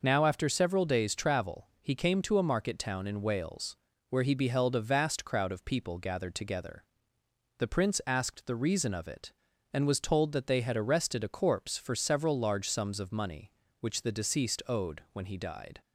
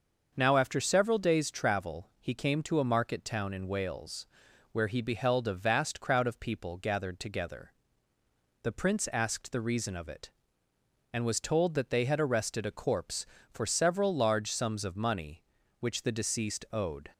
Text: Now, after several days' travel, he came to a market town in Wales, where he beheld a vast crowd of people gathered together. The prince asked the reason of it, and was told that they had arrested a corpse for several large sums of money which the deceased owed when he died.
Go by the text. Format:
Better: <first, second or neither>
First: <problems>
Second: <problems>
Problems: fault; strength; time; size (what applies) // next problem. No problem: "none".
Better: first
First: none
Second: starts louder than the rest; until 1.3 s; 6 dB // stops before "when he died"; at 17.1 s